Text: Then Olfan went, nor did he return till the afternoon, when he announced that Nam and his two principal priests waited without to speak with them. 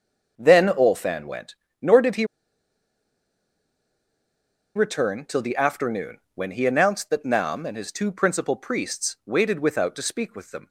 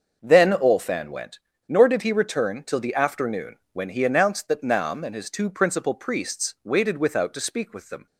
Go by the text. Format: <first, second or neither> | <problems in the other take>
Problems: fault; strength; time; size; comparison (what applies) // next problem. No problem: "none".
second | starts louder than the rest; until 1.3 s; 6.5 dB; also in the second // pauses between "he" and "return"; strong; at 2.2 s; 2.5 s long